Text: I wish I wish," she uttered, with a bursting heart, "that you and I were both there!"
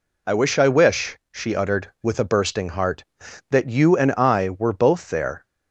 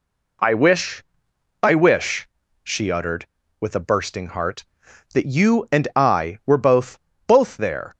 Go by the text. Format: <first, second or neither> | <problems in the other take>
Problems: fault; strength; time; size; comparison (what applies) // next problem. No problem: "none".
first | pauses between "wish" and "I"; noticeable; at 1.0 s; 0.58 s long // says "both" twice; at 7.2 s